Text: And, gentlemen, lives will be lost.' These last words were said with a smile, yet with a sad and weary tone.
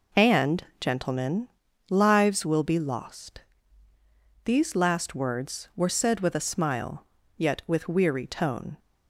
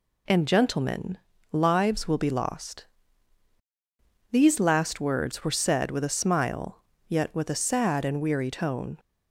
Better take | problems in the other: second | skips "a sad and"; at 7.8 s

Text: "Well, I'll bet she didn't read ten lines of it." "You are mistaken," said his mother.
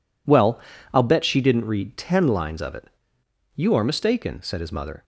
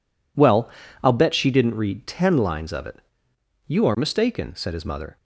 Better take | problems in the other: neither | none

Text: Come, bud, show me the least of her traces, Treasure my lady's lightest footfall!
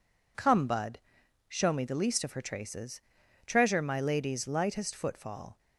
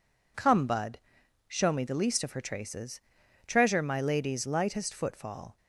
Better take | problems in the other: neither | none

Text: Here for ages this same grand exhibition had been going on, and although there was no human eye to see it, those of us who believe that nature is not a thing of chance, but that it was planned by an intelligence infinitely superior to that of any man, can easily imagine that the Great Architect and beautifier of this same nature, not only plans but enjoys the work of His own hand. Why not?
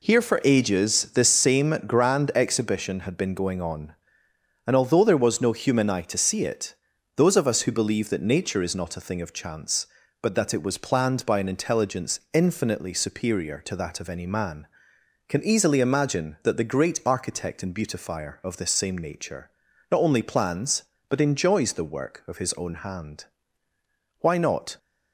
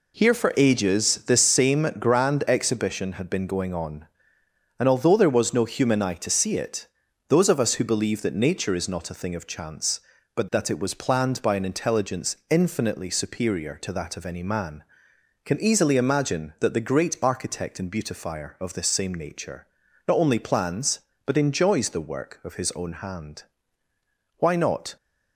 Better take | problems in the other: neither | none

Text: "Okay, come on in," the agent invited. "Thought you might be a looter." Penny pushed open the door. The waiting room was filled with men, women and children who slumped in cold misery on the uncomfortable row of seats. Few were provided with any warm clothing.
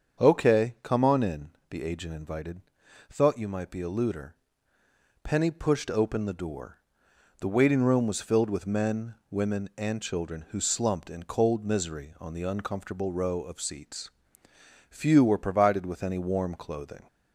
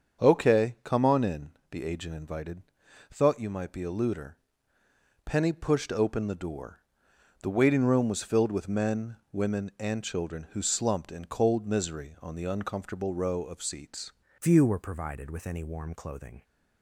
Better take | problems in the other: first | starts louder than the rest; strong; until 1.2 s; 7 dB; also in the first // changes voice at "Few"; from 14.4 s on; 2.0 s long

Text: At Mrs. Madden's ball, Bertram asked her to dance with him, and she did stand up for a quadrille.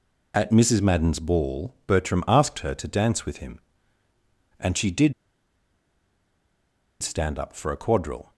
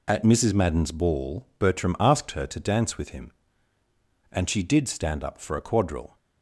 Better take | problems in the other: second | pauses between "did" and "stand"; strong; at 5.1 s; 1.8 s long

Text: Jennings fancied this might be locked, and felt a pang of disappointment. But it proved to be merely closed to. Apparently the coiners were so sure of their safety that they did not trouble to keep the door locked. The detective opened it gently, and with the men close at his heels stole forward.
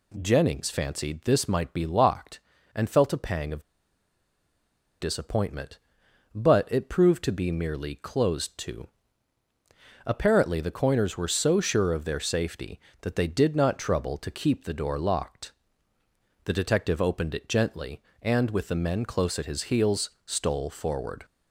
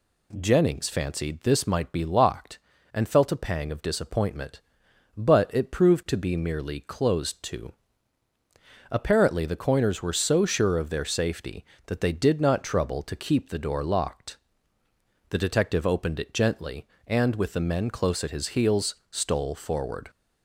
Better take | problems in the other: second | pauses between "of" and "disappointment"; strong; at 3.6 s; 1.3 s long

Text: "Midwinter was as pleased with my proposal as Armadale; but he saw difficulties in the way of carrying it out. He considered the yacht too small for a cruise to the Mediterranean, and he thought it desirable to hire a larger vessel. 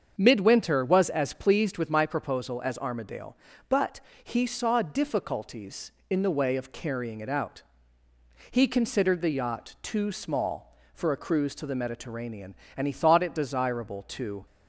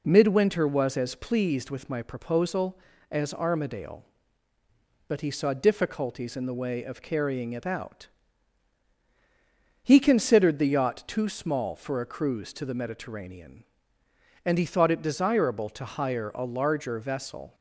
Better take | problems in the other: second | starts louder than the rest; strong; until 1.2 s; 7 dB // pauses between "but" and "he"; slight; at 3.9 s; 0.24 s long // stops before "hire a larger vessel"; at 14.4 s

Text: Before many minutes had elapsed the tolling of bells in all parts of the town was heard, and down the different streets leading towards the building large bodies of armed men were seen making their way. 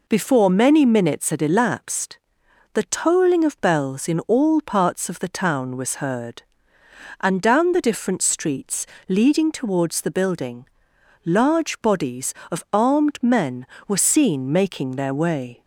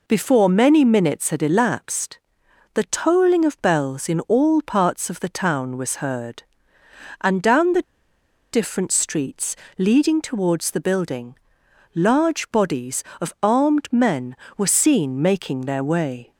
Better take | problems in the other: first | pauses between "elapsed" and "the"; noticeable; at 2.1 s; 0.54 s long; noticeable in the first // pauses between "the" and "different"; noticeable; at 7.8 s; 0.69 s long // pauses between "streets" and "leading"; slight; at 9.5 s; 0.22 s long; slight in the first // pauses between "building" and "large"; noticeable; at 11.3 s; 0.58 s long; noticeable in the first

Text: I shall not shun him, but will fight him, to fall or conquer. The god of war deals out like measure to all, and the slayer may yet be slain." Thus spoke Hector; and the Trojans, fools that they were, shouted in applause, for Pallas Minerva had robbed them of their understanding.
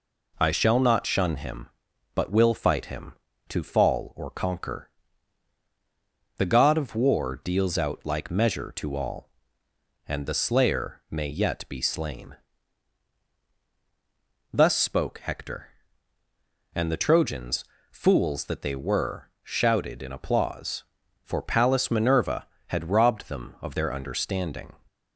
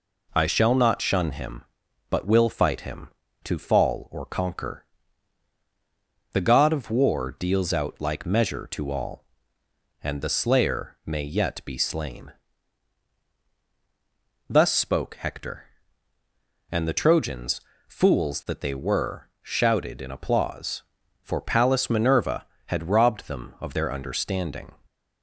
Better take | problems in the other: neither | none

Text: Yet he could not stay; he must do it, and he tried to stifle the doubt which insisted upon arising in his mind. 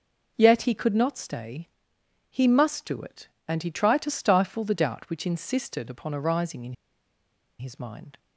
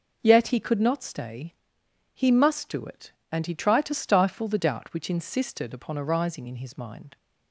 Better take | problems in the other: second | pauses between "in" and "his"; noticeable; at 6.7 s; 0.85 s long

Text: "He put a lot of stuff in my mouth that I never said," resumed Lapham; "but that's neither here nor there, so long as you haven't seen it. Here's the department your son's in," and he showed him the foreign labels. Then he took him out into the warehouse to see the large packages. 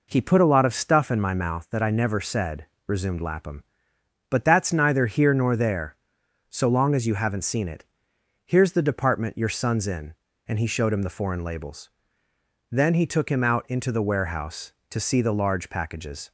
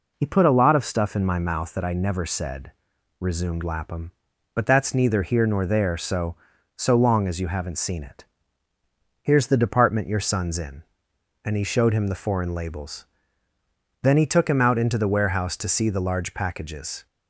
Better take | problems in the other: first | says "so" twice; at 6.7 s

